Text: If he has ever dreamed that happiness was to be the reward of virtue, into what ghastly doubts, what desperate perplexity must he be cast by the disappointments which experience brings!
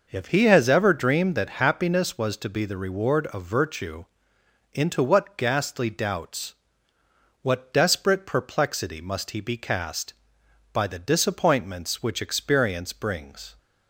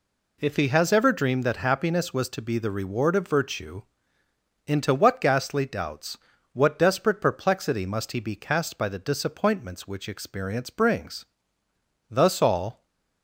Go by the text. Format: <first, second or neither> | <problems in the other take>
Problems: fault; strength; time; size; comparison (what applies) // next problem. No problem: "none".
first | goes on to say "Thus all"; noticeable; from 12.1 s on; 0.74 s long // stays silent after the last word; slight; from 12.7 s on; 0.5 s long